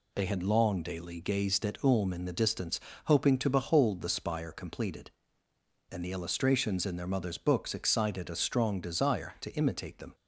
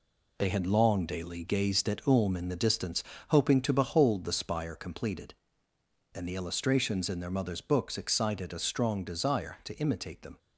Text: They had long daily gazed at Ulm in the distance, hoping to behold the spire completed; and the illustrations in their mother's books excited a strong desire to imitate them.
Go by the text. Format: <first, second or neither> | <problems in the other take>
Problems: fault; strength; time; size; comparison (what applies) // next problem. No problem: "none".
first | gets quieter; noticeable; throughout; 6 dB